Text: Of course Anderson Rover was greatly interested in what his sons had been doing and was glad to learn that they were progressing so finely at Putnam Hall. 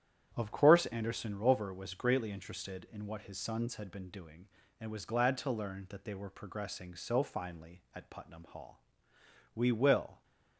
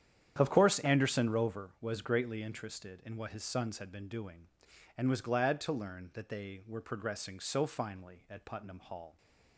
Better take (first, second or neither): second